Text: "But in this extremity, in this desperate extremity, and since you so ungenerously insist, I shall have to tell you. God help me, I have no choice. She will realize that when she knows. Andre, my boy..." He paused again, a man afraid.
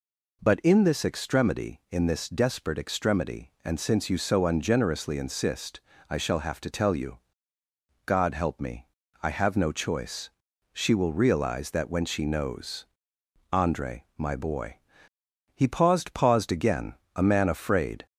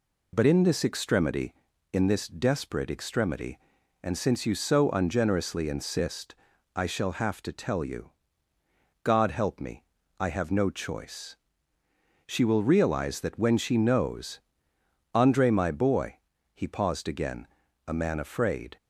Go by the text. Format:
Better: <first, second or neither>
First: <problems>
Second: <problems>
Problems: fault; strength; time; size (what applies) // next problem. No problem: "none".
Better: second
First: says "paused" twice; at 16.1 s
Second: none